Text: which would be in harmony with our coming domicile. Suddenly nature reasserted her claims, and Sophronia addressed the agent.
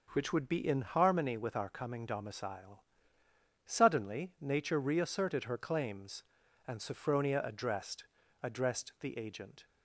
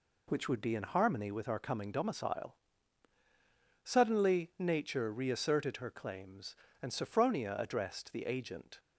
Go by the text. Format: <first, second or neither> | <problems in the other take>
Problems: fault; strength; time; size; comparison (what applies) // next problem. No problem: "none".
second | says "addressed" twice; at 8.4 s